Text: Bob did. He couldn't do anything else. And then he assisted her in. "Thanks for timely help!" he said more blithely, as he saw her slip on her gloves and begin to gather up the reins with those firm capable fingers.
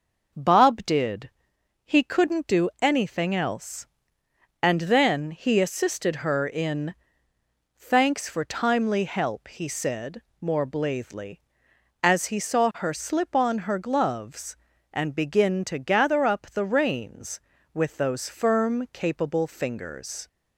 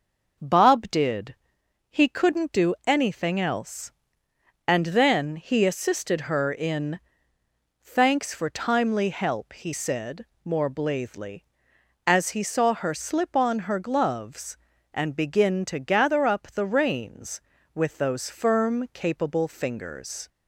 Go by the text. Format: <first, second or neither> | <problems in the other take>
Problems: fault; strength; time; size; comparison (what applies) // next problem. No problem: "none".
neither | pauses between "said" and "more"; slight; the same in both